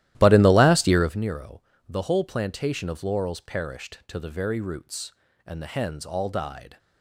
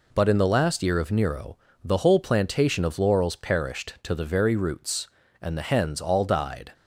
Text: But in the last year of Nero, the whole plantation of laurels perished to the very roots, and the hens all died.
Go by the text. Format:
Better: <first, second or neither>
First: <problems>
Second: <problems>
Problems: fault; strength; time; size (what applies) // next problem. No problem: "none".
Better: second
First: starts louder than the rest; strong; until 1.2 s; 14 dB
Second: none